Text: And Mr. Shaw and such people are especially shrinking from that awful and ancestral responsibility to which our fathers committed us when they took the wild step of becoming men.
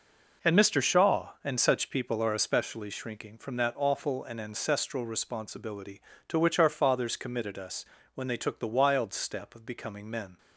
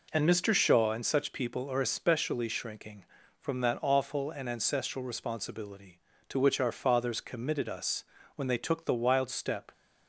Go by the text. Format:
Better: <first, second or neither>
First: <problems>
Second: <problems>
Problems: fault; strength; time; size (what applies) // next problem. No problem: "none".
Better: first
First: pauses between "us" and "when"; slight; at 7.8 s; 0.32 s long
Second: pauses between "us" and "when"; slight; at 8.0 s; 0.32 s long // stops before "of becoming men"; at 9.7 s